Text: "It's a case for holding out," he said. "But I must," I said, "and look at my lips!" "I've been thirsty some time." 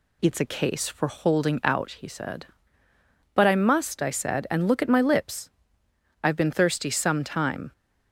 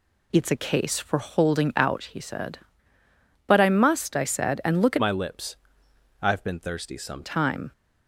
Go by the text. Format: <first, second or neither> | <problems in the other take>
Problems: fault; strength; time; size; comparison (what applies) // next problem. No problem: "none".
first | changes voice from "my" to "some"; from 5.0 to 7.2 s; 2.2 s long